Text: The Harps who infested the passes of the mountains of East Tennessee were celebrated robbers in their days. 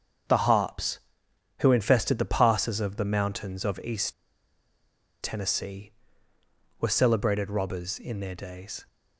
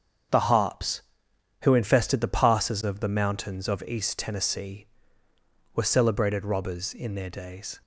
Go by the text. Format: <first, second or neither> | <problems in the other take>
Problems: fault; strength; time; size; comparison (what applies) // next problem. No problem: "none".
second | starts louder than the rest; strong; until 1.9 s; 7 dB; strong in the second // pauses between "East" and "Tennessee"; at 4.1 s; 1.0 s long